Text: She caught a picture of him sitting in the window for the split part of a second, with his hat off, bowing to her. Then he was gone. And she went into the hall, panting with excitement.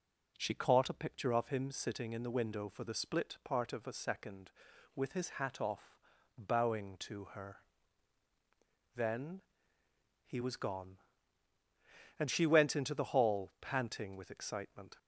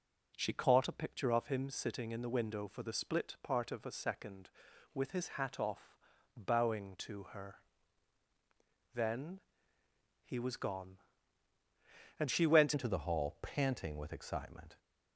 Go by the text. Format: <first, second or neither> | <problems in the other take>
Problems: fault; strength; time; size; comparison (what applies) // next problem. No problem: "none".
first | pauses between "Then" and "he"; noticeable; at 9.3 s; 0.84 s long; noticeable in the first // changes voice at "into"; from 12.7 s on; 2.0 s long